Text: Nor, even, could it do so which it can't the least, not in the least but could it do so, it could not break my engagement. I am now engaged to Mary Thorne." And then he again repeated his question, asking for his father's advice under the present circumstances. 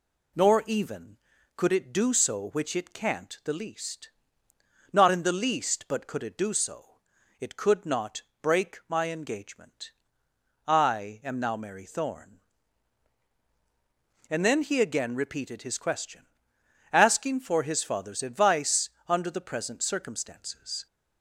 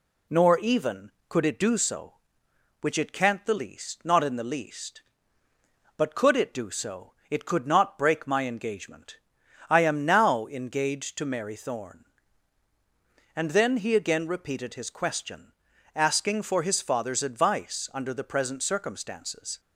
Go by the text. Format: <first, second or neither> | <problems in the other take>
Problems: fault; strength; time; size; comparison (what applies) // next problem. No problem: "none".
second | pauses between "not" and "break"; slight; at 8.2 s; 0.20 s long // skips "engaged to"; at 11.5 s // pauses between "advice" and "under"; slight; at 18.9 s; 0.18 s long